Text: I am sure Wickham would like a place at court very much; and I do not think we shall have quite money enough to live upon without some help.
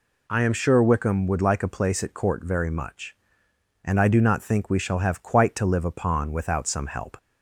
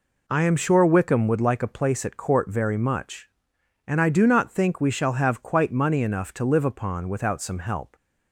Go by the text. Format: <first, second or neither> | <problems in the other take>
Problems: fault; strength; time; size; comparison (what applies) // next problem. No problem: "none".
second | skips "money enough"; at 5.5 s